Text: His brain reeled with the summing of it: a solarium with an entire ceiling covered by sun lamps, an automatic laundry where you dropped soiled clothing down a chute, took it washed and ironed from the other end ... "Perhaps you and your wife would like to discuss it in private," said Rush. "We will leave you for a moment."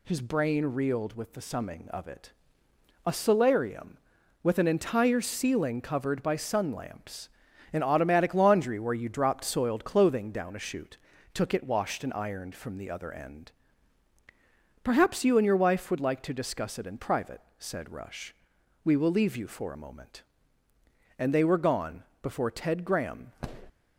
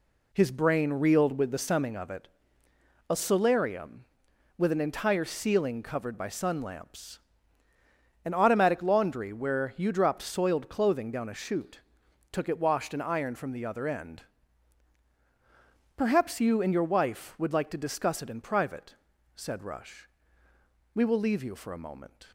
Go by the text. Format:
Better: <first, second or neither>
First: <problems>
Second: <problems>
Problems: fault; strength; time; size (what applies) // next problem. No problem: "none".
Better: second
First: goes on to say "And they were gone before Ted Graham"; strong; from 21.1 s on; 2.1 s long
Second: none